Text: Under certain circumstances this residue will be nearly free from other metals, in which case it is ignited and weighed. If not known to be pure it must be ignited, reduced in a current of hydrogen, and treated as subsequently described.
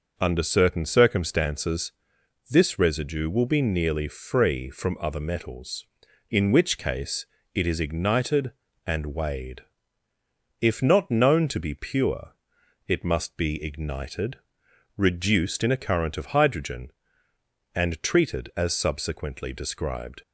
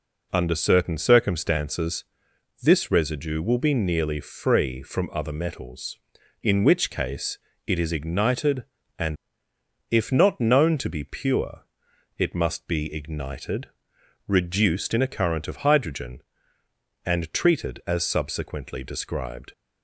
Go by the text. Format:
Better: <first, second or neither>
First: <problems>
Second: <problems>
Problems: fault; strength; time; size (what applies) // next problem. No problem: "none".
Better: first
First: pauses between "circumstances" and "this"; noticeable; at 1.9 s; 0.56 s long // pauses between "case" and "it"; slight; at 7.2 s; 0.28 s long // pauses between "pure" and "it"; noticeable; at 12.3 s; 0.56 s long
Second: pauses between "circumstances" and "this"; noticeable; at 2.0 s; 0.56 s long // pauses between "case" and "it"; slight; at 7.3 s; 0.28 s long // skips "weighed"; at 9.5 s // pauses between "pure" and "it"; noticeable; at 11.6 s; 0.56 s long